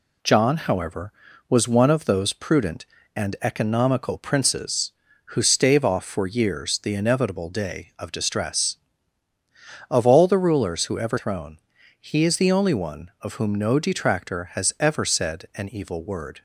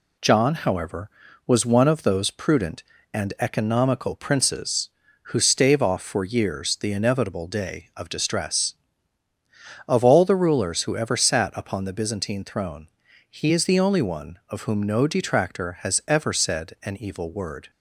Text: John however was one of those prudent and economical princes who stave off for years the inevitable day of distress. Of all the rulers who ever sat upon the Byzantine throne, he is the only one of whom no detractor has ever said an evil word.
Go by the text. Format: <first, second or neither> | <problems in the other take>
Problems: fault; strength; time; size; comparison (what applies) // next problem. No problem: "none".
second | skips "sat upon the Byzantine"; at 11.1 s